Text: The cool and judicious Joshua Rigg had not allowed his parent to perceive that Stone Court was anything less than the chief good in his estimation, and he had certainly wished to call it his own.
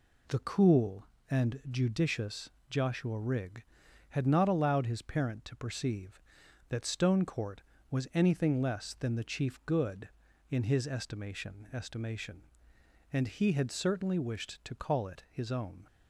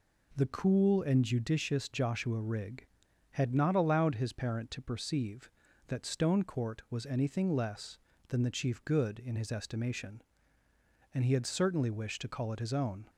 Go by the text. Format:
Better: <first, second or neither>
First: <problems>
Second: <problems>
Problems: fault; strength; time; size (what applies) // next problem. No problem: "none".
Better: second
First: pauses between "judicious" and "Joshua"; slight; at 2.5 s; 0.18 s long // says "estimation" twice; at 11.7 s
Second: none